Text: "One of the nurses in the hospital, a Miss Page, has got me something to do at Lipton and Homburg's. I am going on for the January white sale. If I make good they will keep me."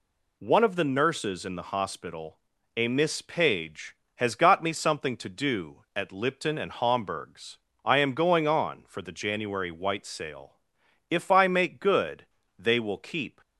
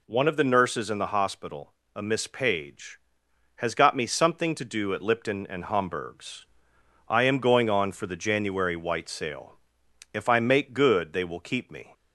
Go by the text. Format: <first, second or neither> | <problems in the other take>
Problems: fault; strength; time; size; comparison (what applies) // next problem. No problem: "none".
second | pauses between "good" and "they"; slight; at 12.2 s; 0.32 s long // stops before "me"; at 13.4 s